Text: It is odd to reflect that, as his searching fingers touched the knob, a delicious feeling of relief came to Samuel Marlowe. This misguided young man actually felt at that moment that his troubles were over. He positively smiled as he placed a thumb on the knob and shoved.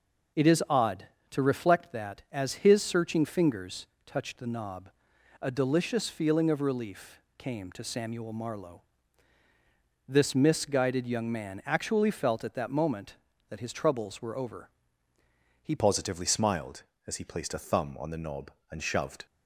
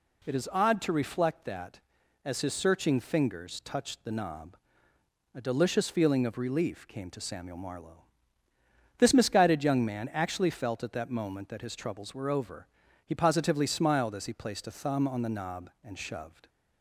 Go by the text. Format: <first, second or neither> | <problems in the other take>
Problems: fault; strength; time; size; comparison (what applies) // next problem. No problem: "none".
second | pauses between "fingers" and "touched"; slight; at 3.8 s; 0.22 s long // pauses between "relief" and "came"; slight; at 7.2 s; 0.16 s long // changes voice at "positively"; from 15.7 s on; 3.5 s long